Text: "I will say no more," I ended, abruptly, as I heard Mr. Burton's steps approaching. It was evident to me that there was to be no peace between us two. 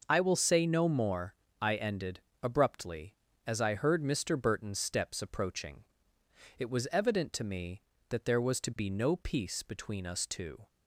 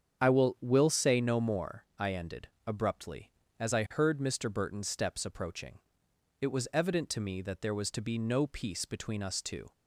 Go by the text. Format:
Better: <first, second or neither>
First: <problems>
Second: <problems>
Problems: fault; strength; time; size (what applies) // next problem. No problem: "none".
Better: first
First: starts louder than the rest; until 1.0 s; 6 dB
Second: starts louder than the rest; strong; until 1.2 s; 7.5 dB // says "will" twice; at 0.5 s